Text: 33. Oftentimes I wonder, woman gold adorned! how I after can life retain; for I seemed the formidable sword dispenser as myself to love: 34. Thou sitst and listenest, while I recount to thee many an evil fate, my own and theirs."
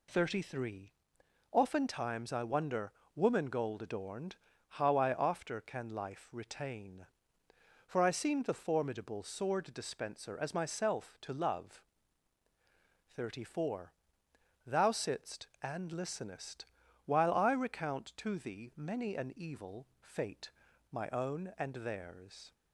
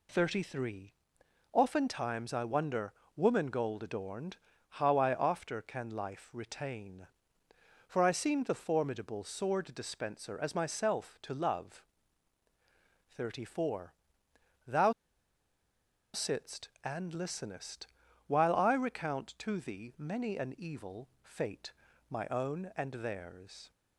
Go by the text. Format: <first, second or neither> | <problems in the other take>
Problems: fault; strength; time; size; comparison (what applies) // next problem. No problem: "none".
first | pauses between "Thou" and "sitst"; at 14.9 s; 1.2 s long // pauses between "evil" and "fate"; slight; at 21.0 s; 0.16 s long; slight in the first